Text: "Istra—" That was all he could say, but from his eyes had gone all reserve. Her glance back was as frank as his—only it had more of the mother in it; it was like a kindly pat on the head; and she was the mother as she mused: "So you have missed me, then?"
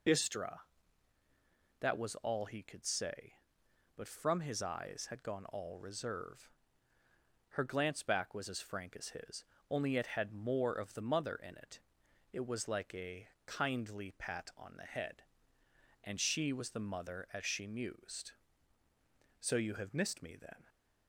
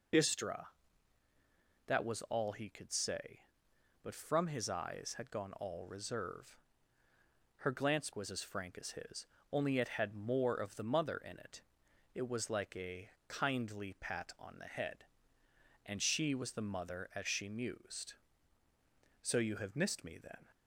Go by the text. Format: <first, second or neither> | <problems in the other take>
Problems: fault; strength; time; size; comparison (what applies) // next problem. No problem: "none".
first | skips "back"; at 8.1 s // pauses between "a" and "kindly"; slight; at 13.0 s; 0.20 s long; slight in the first